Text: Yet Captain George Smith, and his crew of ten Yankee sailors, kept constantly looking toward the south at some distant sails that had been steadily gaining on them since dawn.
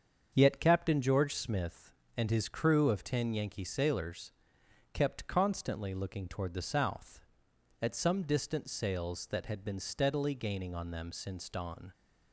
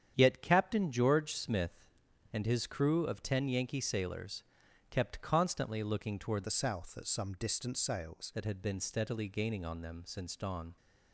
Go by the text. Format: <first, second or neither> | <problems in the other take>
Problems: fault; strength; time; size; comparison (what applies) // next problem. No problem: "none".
first | starts louder than the rest; strong; until 1.1 s; 9 dB; strong in the first // changes voice from "the" to "sails"; from 6.4 to 8.3 s; 1.9 s long